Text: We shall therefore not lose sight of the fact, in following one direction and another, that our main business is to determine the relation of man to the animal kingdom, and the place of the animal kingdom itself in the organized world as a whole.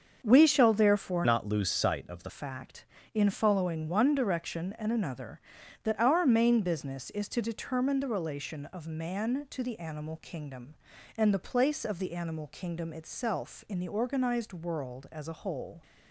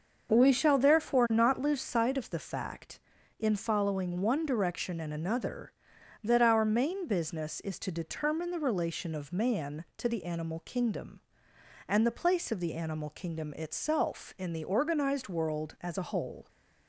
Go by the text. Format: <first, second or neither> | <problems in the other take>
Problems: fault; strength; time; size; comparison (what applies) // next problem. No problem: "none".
second | starts louder than the rest; until 1.2 s; 6.5 dB; also in the second // changes voice from "not" to "the"; from 1.2 to 2.2 s; 1.0 s long